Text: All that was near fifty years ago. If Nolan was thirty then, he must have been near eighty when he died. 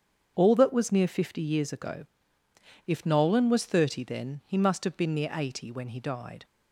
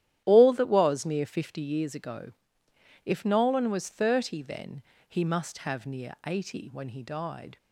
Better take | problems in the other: first | starts louder than the rest; strong; until 1.2 s; 11.5 dB; strong in the first // skips "been"; at 5.8 s

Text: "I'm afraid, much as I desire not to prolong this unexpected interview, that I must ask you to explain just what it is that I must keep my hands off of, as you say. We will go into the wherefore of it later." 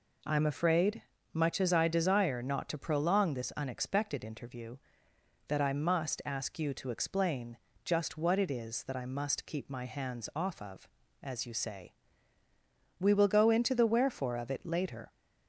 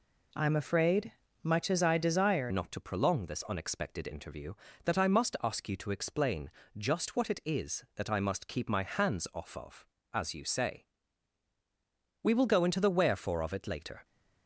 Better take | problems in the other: first | changes voice at "not"; from 2.5 s on; 11.5 s long // pauses between "explain" and "just"; slight; at 6.5 s; 0.26 s long; slight in the first

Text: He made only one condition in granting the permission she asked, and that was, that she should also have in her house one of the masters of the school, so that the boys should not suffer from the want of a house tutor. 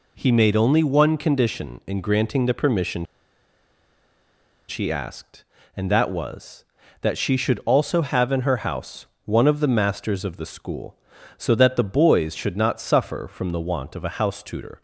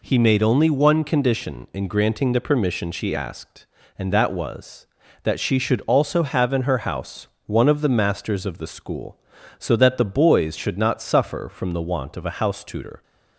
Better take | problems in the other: second | pauses between "permission" and "she"; strong; at 3.0 s; 1.6 s long // pauses between "house" and "one"; slight; at 9.0 s; 0.18 s long; slight in the second

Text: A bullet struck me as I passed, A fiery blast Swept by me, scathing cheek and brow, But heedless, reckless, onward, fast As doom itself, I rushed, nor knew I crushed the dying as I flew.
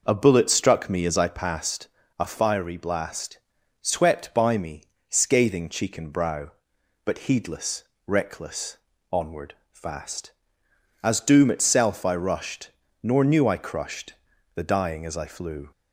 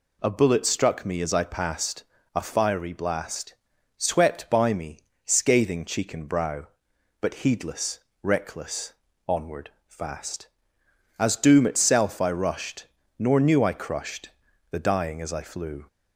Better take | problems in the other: second | starts louder than the rest; noticeable; until 1.3 s; 5.5 dB // pauses between "blast" and "Swept"; noticeable; at 3.3 s; 0.46 s long; noticeable in the second // pauses between "crushed" and "the"; at 14.1 s; 0.40 s long; also in the second

